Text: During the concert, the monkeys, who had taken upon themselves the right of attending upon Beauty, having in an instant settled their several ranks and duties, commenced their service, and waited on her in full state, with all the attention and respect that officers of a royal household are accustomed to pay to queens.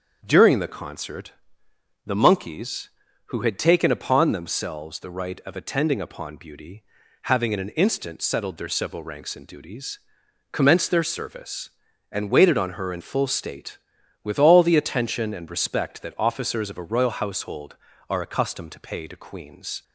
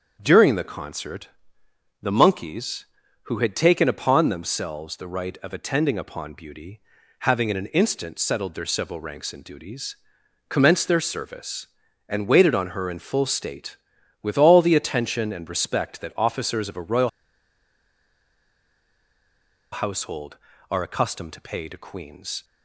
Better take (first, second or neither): first